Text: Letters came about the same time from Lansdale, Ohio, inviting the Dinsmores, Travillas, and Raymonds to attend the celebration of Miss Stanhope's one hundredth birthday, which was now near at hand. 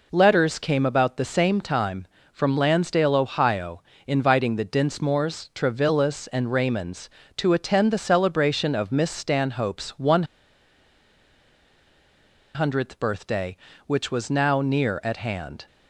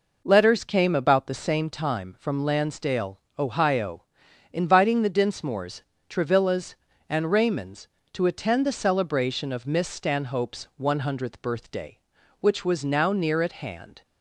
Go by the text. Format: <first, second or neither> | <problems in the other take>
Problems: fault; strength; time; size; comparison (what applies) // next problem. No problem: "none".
second | pauses between "one" and "hundredth"; strong; at 10.2 s; 2.3 s long